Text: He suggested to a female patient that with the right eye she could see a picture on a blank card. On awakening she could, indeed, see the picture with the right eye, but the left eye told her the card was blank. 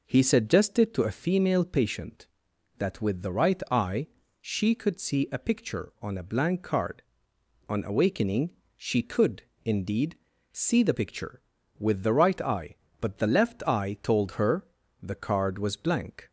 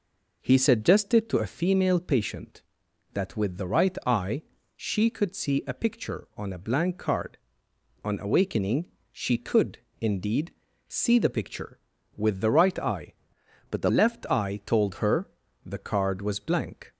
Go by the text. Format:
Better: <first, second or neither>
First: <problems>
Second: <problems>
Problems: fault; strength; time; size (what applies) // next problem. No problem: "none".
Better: first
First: pauses between "eye" and "she"; slight; at 4.0 s; 0.34 s long // pauses between "awakening" and "she"; slight; at 8.5 s; 0.24 s long // pauses between "her" and "the"; slight; at 14.6 s; 0.36 s long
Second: pauses between "eye" and "she"; slight; at 4.4 s; 0.34 s long // pauses between "awakening" and "she"; slight; at 8.8 s; 0.24 s long // changes voice from "but" to "the"; from 13.6 to 13.8 s; 0.2 s long // pauses between "her" and "the"; slight; at 15.2 s; 0.36 s long